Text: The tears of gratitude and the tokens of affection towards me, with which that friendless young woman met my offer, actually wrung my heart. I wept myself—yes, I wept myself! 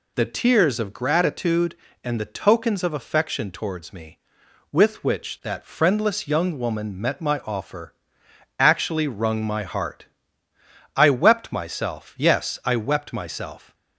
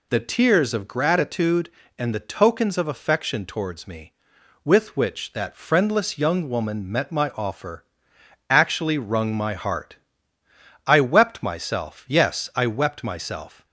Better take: neither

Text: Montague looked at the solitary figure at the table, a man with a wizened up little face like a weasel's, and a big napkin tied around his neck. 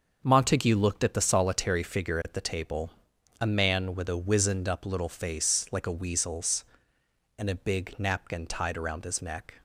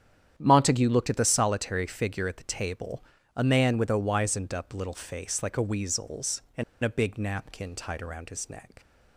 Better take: first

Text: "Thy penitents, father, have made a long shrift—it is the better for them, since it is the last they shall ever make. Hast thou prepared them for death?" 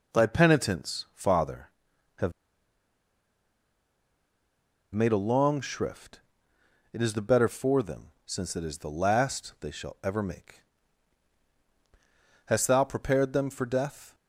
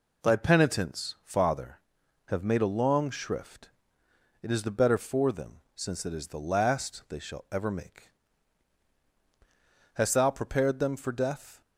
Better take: second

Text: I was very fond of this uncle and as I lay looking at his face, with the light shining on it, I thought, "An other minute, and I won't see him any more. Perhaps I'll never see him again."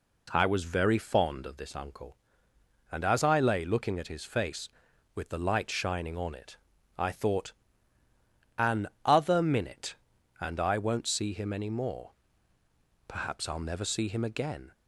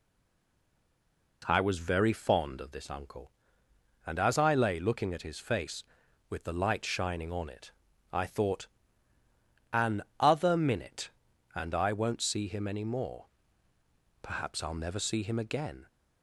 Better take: first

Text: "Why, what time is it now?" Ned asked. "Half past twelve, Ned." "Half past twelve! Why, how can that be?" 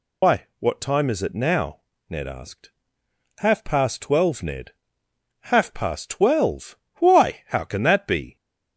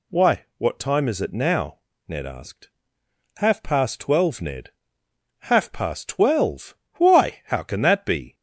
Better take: second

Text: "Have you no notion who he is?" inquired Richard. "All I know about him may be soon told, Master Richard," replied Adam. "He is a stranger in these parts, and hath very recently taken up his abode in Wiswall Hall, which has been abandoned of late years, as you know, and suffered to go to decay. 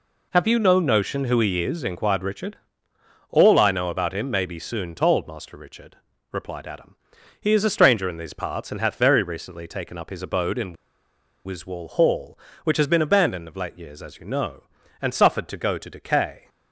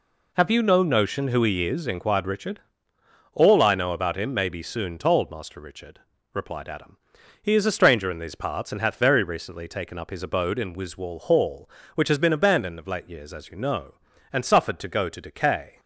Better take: second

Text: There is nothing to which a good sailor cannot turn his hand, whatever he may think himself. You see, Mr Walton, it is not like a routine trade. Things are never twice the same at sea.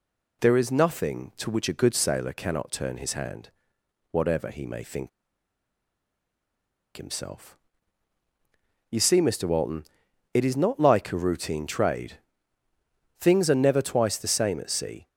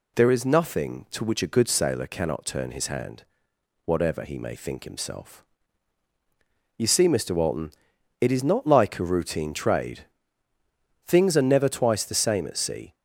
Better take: second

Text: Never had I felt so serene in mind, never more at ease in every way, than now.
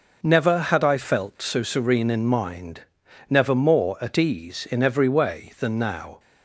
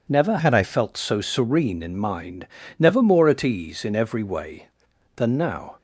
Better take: first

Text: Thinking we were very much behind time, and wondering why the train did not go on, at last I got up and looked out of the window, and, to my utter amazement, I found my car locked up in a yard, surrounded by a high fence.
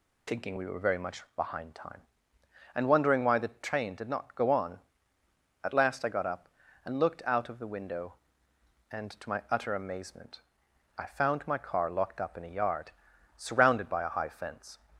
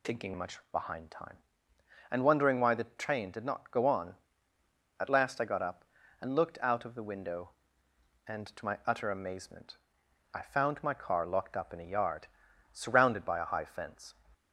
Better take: first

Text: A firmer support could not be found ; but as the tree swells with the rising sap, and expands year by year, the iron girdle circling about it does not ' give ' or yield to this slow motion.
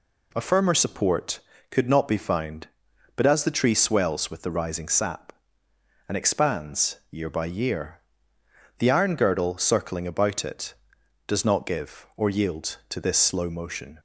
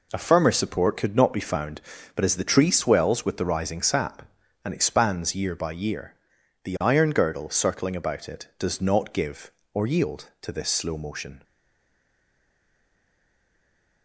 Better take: first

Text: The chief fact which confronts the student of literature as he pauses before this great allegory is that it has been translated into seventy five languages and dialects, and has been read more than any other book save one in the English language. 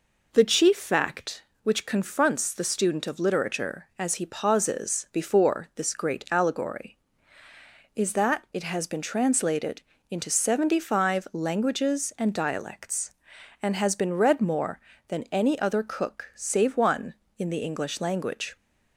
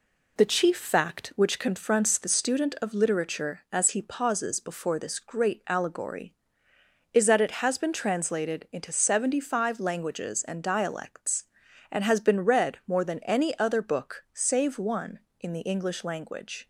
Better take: second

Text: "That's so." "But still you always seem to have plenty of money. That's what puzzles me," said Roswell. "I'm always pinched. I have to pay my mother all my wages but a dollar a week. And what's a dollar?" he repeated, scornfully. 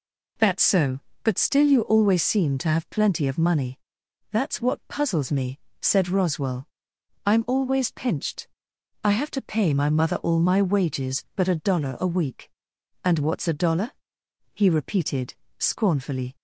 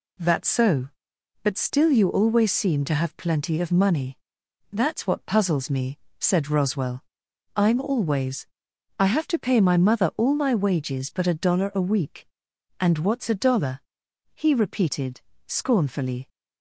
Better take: first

